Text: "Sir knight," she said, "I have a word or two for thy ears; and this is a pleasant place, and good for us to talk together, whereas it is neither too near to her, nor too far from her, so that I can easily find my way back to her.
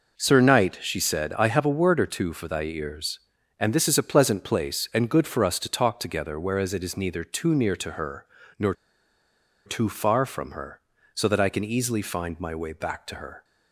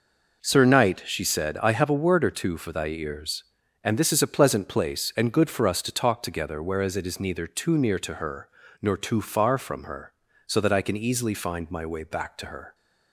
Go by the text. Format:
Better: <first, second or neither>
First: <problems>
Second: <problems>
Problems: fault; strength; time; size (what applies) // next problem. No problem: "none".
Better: second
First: pauses between "nor" and "too"; noticeable; at 8.7 s; 0.92 s long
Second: none